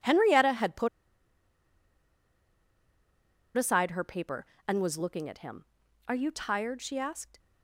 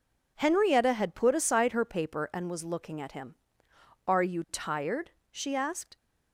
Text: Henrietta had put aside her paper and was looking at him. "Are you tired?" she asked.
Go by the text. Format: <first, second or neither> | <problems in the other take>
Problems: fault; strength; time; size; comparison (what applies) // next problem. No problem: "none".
second | pauses between "put" and "aside"; strong; at 0.8 s; 2.6 s long